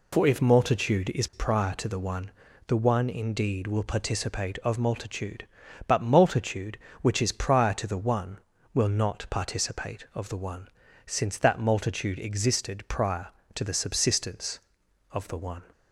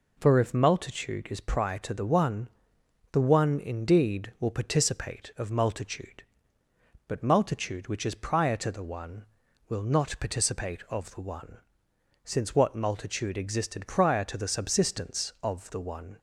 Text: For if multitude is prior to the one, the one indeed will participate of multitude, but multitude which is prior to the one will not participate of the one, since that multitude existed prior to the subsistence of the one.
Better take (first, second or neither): first